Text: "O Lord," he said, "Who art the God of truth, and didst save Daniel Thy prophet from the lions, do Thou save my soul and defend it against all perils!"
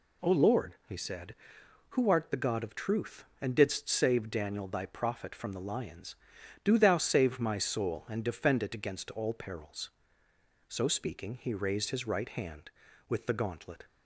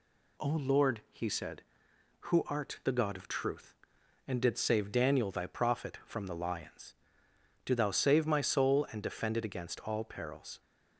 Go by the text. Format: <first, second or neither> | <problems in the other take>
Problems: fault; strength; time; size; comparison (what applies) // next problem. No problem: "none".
second | goes on to say "So speaking he raised his right hand with the gauntlet"; strong; from 10.6 s on; 3.1 s long